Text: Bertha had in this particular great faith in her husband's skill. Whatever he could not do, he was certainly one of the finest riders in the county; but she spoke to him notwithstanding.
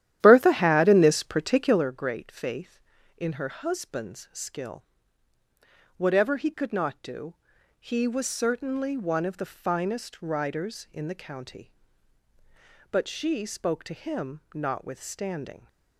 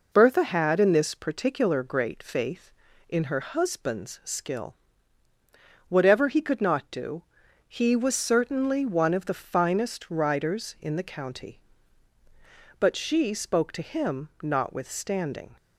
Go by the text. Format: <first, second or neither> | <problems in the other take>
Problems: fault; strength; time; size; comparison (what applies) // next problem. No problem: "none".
second | starts louder than the rest; strong; until 1.9 s; 12 dB